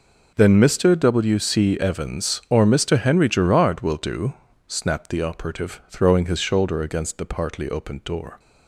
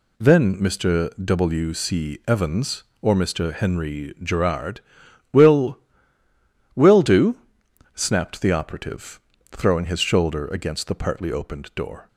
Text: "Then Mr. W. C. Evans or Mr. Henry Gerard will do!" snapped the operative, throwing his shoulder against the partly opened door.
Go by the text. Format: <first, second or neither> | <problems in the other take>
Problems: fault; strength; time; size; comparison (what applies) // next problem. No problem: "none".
first | says "will" twice; at 6.7 s